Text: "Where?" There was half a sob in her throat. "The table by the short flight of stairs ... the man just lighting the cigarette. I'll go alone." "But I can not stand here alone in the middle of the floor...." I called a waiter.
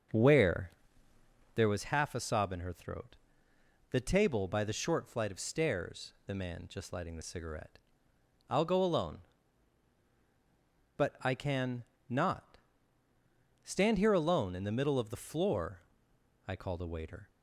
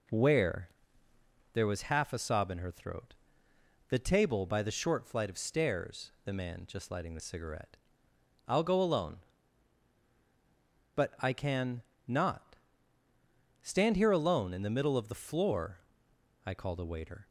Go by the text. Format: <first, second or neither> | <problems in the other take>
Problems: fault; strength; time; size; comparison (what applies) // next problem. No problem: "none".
second | starts louder than the rest; until 1.8 s; 6.5 dB // pauses between "can" and "not"; slight; at 11.8 s; 0.24 s long; slight in the second // pauses between "not" and "stand"; at 12.5 s; 1.0 s long; also in the second